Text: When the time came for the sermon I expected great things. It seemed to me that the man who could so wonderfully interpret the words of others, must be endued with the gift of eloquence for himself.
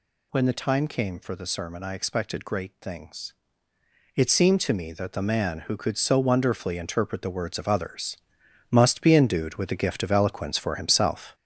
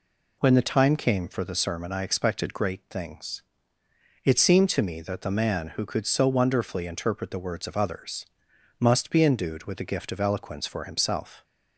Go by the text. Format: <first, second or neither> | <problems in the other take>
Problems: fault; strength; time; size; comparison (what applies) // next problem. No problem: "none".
second | gets louder; noticeable; throughout; 5 dB